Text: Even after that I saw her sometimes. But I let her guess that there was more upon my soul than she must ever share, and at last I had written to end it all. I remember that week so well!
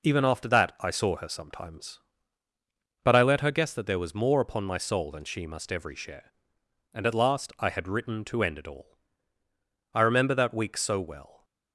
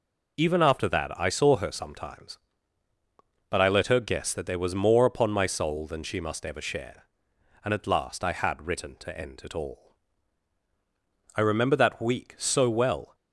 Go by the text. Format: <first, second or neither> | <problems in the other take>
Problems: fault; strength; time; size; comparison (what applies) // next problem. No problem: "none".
second | says "every" for "ever"; at 5.7 s